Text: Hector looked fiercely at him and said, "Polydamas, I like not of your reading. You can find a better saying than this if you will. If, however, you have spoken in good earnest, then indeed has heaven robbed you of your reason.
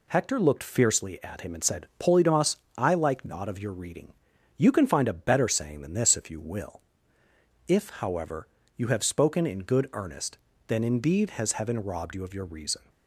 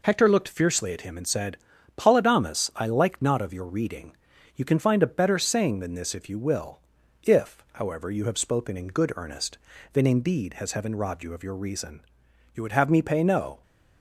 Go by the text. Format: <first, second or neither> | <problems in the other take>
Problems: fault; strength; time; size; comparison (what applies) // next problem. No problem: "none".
first | goes on to say "You would have me pay no"; noticeable; from 12.5 s on; 1.0 s long